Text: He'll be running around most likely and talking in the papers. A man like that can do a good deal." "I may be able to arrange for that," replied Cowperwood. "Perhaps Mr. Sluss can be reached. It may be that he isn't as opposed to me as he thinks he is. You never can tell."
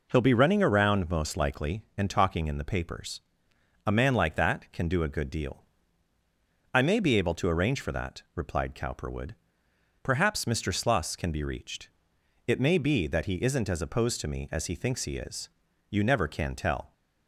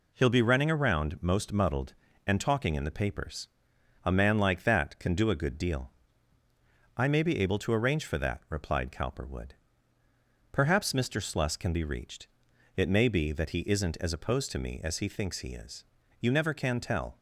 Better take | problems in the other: first | says "muddled" for "likely"; at 1.5 s

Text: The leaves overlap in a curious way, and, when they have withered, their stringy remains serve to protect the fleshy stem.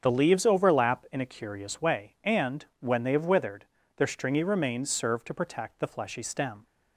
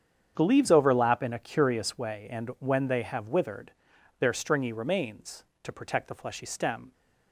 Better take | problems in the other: first | starts louder than the rest; strong; until 1.3 s; 8 dB; strong in the first // skips "serve"; at 5.5 s

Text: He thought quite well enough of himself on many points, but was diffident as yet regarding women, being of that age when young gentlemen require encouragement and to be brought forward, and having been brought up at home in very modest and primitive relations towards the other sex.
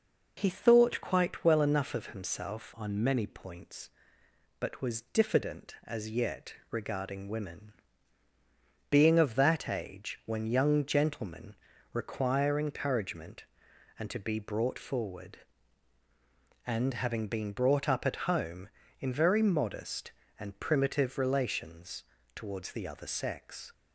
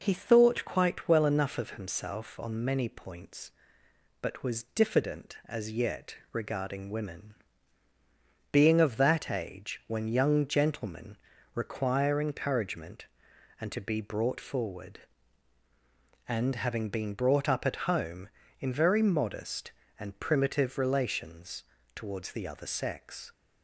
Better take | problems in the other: second | changes voice from "on" to "many"; from 2.7 to 3.2 s; 0.5 s long // pauses between "yet" and "regarding"; slight; at 6.5 s; 0.16 s long; slight in the second // pauses between "gentlemen" and "require"; at 11.5 s; 0.38 s long; also in the second // pauses between "relations" and "towards"; slight; at 22.0 s; 0.32 s long; slight in the second

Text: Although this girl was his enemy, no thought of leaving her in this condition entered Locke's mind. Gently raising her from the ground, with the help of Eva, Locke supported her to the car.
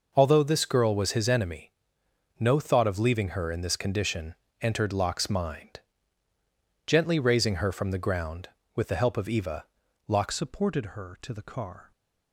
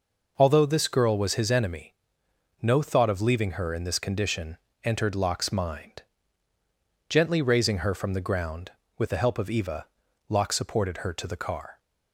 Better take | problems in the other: second | pauses between "condition" and "entered"; slight; at 4.3 s; 0.26 s long; slight in the second // changes voice at "supported"; from 10.3 s on; 1.6 s long

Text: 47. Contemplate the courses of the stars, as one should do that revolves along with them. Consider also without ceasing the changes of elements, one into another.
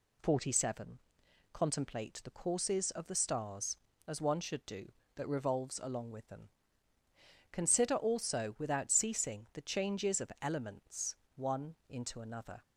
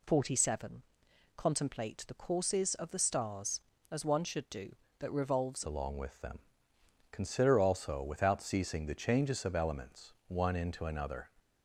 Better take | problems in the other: first | changes voice at "along"; from 5.6 s on; 5.6 s long

